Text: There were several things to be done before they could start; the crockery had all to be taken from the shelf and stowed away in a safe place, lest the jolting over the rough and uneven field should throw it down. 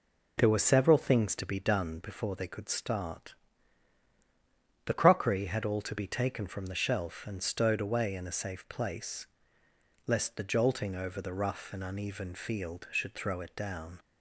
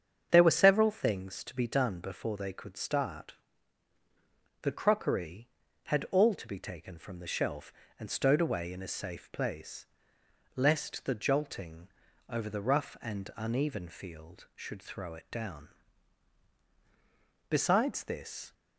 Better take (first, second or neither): first